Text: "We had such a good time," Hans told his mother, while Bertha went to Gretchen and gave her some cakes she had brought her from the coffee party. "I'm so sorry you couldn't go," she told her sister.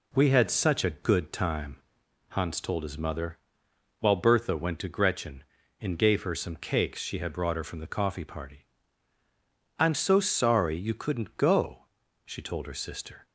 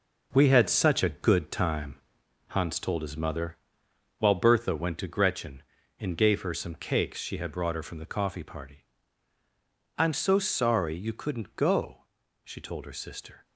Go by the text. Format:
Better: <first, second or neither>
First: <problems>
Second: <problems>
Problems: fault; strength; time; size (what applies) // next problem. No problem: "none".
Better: first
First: none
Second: gets quieter; strong; throughout; 7.5 dB